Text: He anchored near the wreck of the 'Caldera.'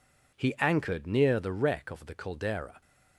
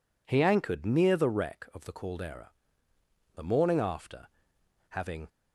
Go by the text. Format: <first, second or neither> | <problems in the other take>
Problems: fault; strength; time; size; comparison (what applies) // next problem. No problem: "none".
first | goes on to say "The morning after having"; strong; from 3.3 s on; 1.9 s long